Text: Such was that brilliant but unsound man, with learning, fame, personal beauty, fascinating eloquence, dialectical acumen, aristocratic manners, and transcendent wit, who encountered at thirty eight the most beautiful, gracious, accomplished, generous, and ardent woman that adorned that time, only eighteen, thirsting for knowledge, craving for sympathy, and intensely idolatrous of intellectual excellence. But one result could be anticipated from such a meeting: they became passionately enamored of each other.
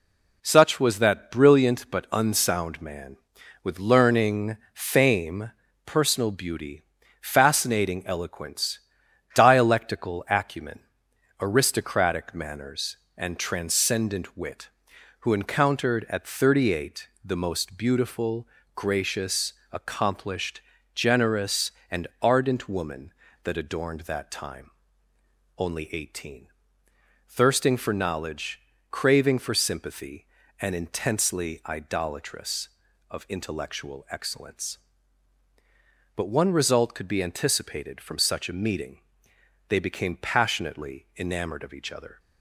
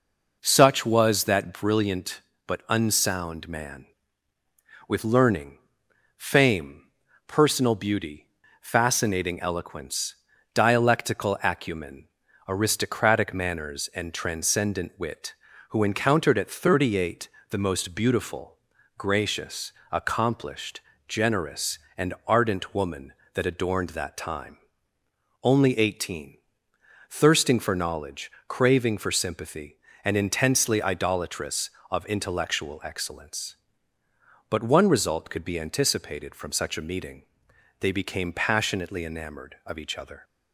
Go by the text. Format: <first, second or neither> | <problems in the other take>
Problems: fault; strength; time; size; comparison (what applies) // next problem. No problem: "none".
neither | pauses between "eight" and "the"; slight; the same in both